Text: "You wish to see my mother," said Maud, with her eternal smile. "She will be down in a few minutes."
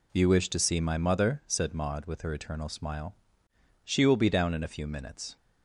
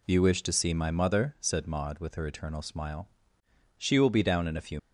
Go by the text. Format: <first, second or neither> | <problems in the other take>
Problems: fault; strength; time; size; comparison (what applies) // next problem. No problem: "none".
first | stops before "minutes"; at 4.7 s